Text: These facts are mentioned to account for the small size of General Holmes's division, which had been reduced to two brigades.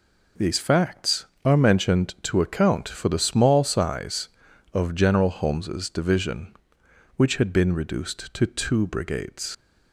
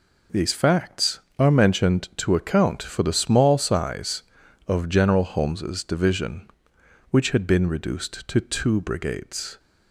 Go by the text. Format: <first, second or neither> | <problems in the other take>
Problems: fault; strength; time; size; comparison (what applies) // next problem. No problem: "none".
second | leaves "brigades" unfinished; at 9.5 s; 95 ms